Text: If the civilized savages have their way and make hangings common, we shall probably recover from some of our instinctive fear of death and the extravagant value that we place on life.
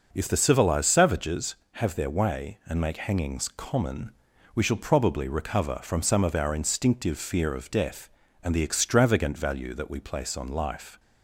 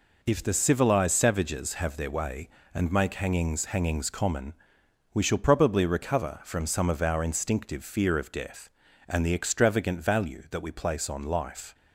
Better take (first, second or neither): first